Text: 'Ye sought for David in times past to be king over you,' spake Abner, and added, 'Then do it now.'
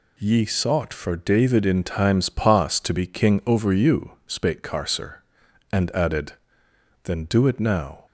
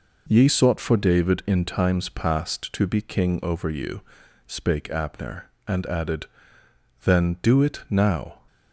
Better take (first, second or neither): second